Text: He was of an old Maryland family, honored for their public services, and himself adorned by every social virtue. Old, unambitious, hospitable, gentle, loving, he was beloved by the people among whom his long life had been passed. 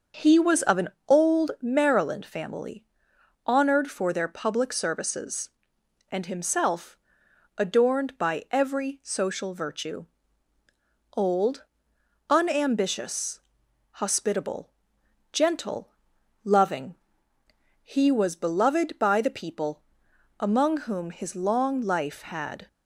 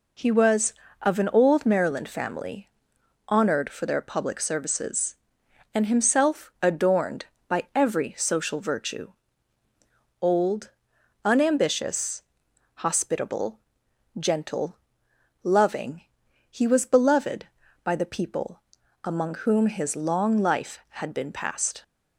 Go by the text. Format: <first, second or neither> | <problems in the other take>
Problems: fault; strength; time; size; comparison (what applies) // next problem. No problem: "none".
second | starts louder than the rest; until 1.3 s; 6.5 dB // pauses between "an" and "old"; slight; at 0.8 s; 0.22 s long // pauses between "himself" and "adorned"; noticeable; at 6.9 s; 0.60 s long // pauses between "people" and "among"; noticeable; at 19.8 s; 0.58 s long; also in the second // stops before "been passed"; at 22.6 s